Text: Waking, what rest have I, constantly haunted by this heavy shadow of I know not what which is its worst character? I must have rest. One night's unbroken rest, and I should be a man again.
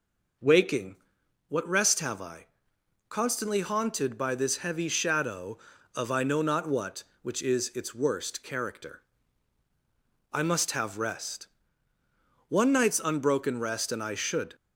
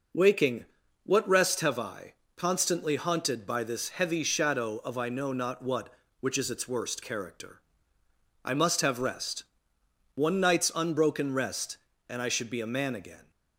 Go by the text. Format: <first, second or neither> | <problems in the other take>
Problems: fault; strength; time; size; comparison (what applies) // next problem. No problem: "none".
second | stops before "be a man again"; at 14.5 s